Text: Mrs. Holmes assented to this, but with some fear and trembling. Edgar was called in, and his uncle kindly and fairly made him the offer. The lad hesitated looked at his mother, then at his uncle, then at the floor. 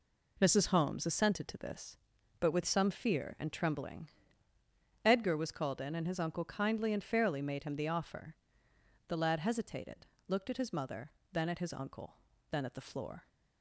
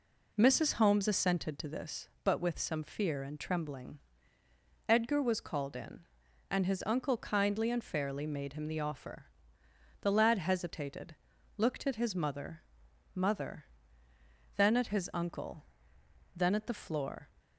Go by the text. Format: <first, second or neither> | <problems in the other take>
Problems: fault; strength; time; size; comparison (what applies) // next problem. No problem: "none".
first | pauses between "hesitated" and "looked"; at 11.1 s; 0.44 s long; slight in the first // says "mother" twice; at 13.1 s